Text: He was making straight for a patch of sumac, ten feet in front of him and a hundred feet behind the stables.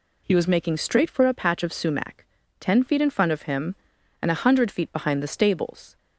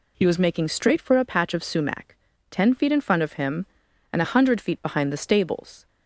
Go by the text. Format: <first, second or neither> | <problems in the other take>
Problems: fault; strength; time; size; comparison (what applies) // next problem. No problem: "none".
neither | none